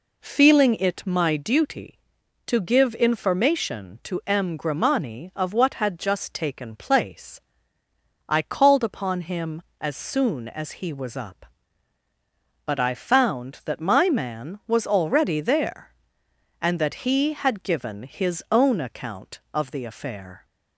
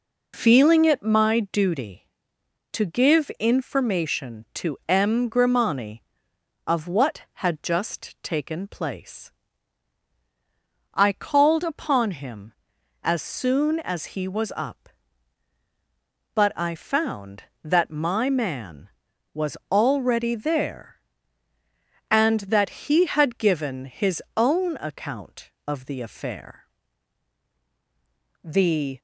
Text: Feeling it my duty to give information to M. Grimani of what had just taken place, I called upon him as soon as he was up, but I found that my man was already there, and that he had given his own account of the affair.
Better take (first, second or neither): first